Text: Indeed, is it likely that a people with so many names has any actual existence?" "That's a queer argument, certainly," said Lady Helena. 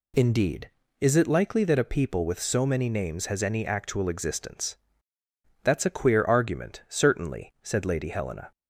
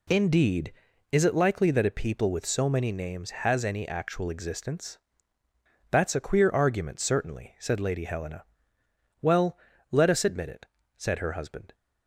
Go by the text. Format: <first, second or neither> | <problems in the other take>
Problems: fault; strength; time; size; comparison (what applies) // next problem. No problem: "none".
first | goes on to say "Well let us admit it said her husband"; strong; from 9.2 s on; 2.5 s long